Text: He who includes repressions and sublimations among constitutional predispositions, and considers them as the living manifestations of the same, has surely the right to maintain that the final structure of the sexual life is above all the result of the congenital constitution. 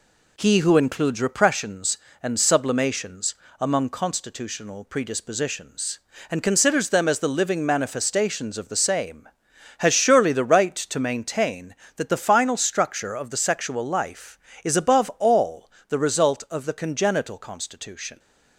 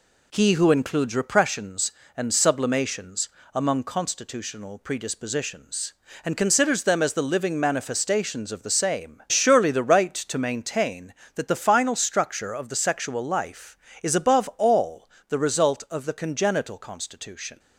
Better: first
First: pauses between "sublimations" and "among"; slight; at 3.3 s; 0.24 s long // pauses between "all" and "the"; slight; at 15.6 s; 0.18 s long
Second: pauses between "sublimations" and "among"; slight; at 3.2 s; 0.24 s long // skips "has"; at 9.2 s // pauses between "all" and "the"; slight; at 15.0 s; 0.20 s long

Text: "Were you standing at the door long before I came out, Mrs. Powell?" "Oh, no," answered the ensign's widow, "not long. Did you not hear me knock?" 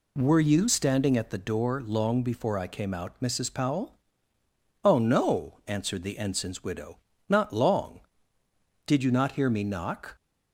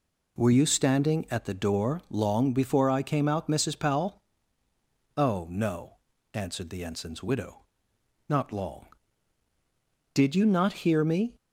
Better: first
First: none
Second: stops before "knock"; at 11.3 s

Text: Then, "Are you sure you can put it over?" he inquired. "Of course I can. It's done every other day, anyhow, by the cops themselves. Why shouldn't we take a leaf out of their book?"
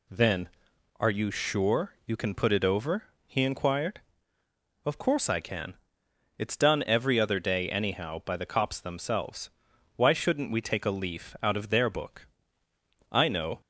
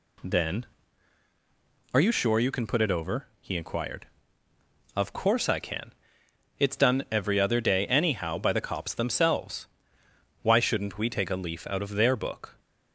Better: second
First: goes on to say "I know"; slight; from 13.1 s on; 0.48 s long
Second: none

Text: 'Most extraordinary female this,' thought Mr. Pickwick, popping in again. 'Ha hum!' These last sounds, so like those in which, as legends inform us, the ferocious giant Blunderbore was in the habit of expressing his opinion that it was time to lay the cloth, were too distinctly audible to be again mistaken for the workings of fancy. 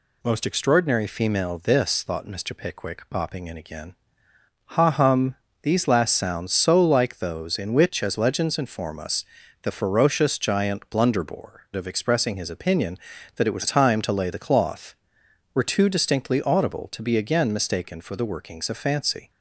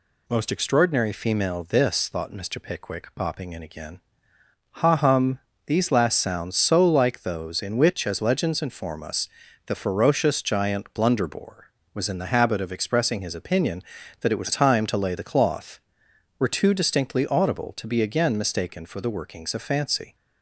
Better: second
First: skips "was in the habit"; at 11.7 s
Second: none

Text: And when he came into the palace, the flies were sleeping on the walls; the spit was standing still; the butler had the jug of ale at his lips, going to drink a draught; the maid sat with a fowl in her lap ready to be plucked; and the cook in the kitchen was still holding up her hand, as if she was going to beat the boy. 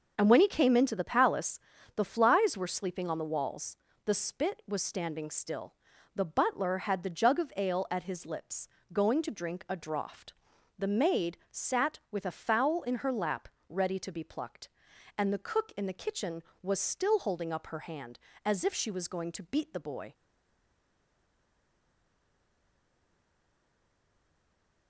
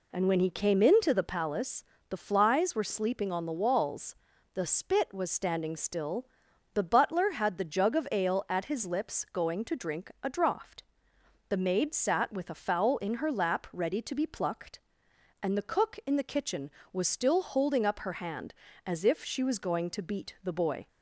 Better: second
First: pauses between "maid" and "sat"; slight; at 11.3 s; 0.16 s long // pauses between "lap" and "ready"; slight; at 13.4 s; 0.18 s long // stays silent after the last word; strong; from 20.1 s on; 4.7 s long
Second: none

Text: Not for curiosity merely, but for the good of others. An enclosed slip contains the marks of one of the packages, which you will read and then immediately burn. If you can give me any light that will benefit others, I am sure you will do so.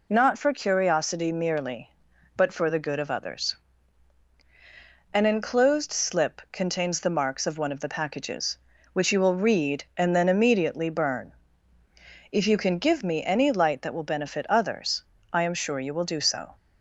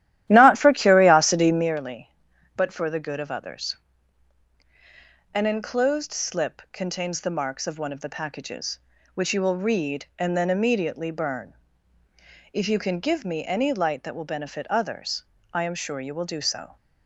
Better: first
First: none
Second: starts louder than the rest; strong; until 1.8 s; 13 dB

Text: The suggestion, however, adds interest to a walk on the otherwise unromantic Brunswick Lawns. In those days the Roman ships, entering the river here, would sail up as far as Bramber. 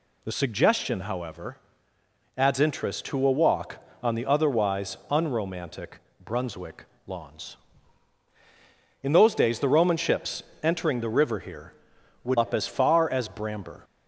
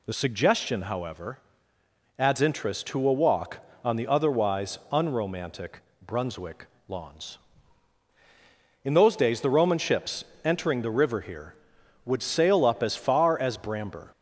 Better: second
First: pauses between "unromantic" and "Brunswick"; slight; at 5.9 s; 0.24 s long // pauses between "Brunswick" and "Lawns"; slight; at 6.8 s; 0.22 s long // skips "sail"; at 12.3 s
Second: pauses between "unromantic" and "Brunswick"; slight; at 5.7 s; 0.24 s long // pauses between "Brunswick" and "Lawns"; slight; at 6.6 s; 0.22 s long

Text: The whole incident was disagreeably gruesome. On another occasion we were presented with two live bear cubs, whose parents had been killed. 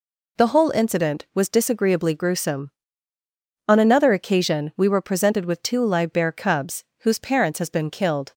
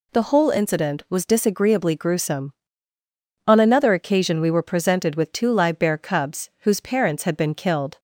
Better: second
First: says "has" for "had"; at 7.5 s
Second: none

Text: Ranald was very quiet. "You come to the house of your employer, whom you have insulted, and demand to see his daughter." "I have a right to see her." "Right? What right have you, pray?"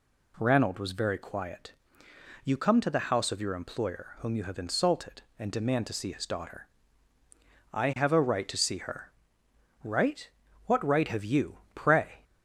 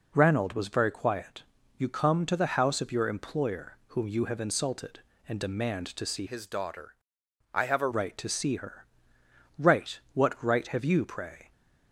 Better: first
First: none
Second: changes voice from "his" to "a"; from 6.2 to 7.9 s; 1.7 s long

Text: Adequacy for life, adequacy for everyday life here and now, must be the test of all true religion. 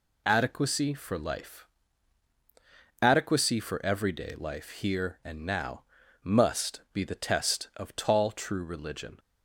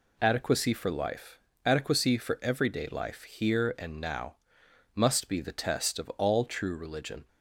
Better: second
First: says "tall" for "all"; at 7.9 s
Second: none

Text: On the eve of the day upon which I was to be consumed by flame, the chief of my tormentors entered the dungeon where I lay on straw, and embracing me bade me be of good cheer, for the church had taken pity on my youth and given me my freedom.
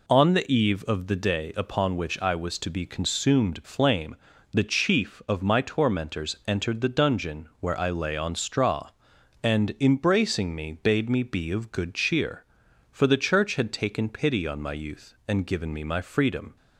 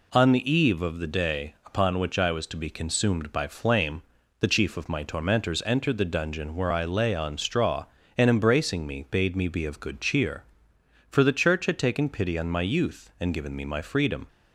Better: second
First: skips "by"; at 3.6 s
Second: none

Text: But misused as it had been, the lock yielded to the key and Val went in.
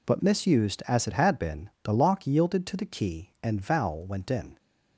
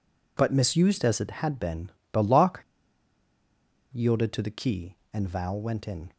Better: first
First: none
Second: pauses between "lock" and "yielded"; strong; at 2.6 s; 1.2 s long

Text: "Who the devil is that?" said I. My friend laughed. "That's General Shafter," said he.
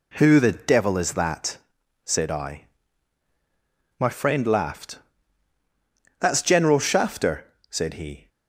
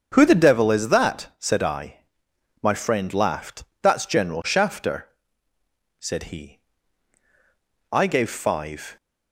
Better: first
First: none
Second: starts louder than the rest; until 1.1 s; 7 dB // goes on to say "I gave five"; noticeable; from 7.9 s on; 1.0 s long

